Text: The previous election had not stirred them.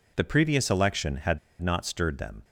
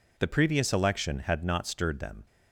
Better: second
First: pauses between "had" and "not"; slight; at 1.3 s; 0.23 s long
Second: none

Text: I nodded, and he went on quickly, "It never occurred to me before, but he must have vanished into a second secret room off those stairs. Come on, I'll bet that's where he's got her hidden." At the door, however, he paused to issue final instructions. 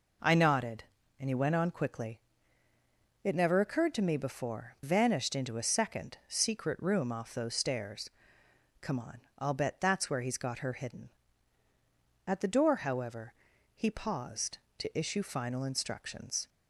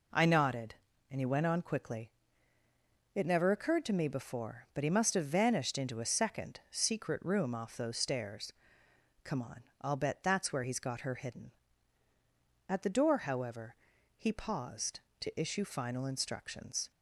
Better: second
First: skips "but he must have"; at 4.7 s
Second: none

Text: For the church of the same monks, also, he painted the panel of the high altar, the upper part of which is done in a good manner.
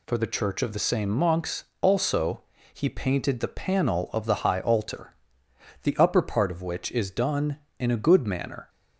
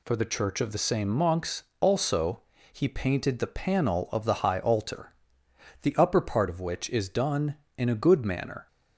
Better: neither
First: none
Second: none

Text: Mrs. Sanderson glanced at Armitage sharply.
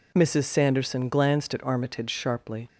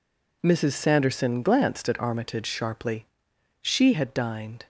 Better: first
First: none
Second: goes on to say "She had dined"; noticeable; from 3.6 s on; 1.0 s long

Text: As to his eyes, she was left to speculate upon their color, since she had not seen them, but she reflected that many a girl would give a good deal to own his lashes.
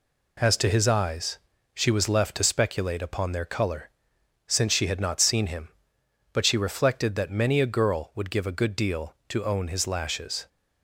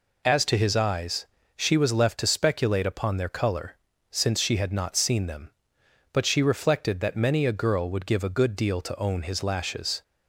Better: second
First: says "him" for "them"; at 5.4 s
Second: none

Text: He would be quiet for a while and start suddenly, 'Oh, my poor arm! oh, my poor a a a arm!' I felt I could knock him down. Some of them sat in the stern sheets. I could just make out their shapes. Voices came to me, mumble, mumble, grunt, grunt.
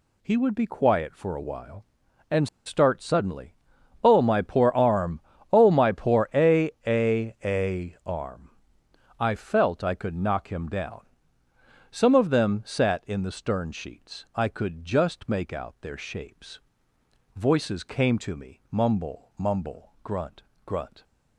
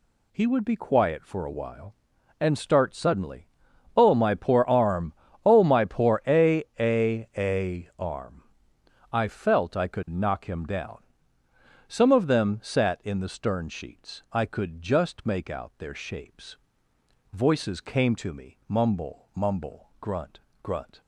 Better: second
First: pauses between "and" and "start"; slight; at 2.4 s; 0.19 s long // pauses between "a" and "a"; slight; at 6.6 s; 0.16 s long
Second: pauses between "a" and "a"; slight; at 6.6 s; 0.16 s long

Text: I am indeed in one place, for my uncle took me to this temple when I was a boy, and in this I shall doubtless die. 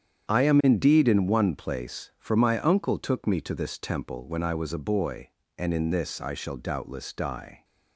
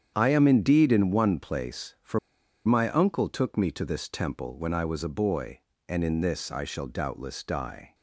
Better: first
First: starts louder than the rest; strong; until 1.3 s; 8.5 dB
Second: starts louder than the rest; strong; until 1.1 s; 8.5 dB // pauses between "for" and "my"; noticeable; at 2.1 s; 0.47 s long

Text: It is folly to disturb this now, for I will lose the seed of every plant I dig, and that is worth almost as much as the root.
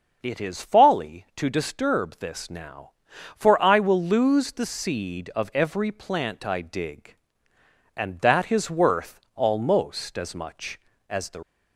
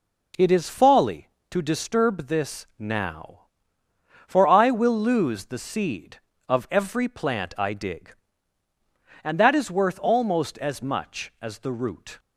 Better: second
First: starts louder than the rest; until 1.2 s; 6.5 dB // pauses between "worth" and "almost"; slight; at 9.2 s; 0.16 s long // stops before "root"; at 11.4 s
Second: none

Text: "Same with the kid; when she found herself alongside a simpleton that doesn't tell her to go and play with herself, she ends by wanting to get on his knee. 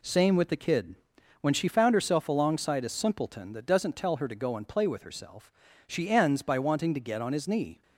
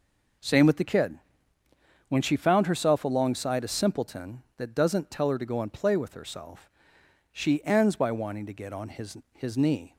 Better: first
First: none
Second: says "his" twice; at 9.3 s

